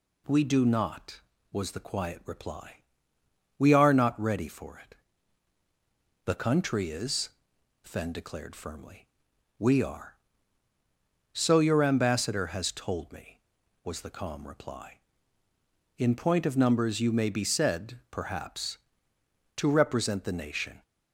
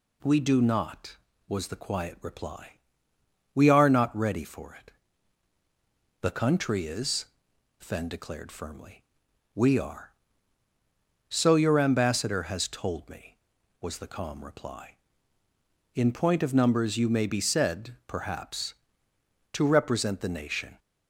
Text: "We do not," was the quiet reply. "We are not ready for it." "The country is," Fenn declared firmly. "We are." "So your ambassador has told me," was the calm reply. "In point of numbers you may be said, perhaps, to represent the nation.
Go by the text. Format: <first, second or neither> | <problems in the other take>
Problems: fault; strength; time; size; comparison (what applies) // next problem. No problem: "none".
neither | none